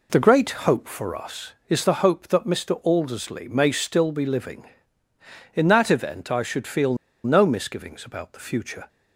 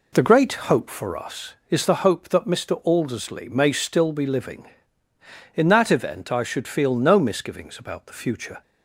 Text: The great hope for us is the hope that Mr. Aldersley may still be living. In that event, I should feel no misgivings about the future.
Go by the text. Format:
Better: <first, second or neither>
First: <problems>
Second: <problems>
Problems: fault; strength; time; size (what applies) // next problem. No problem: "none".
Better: second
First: pauses between "great" and "hope"; slight; at 0.4 s; 0.18 s long // pauses between "feel" and "no"; slight; at 6.9 s; 0.29 s long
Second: pauses between "great" and "hope"; slight; at 0.5 s; 0.18 s long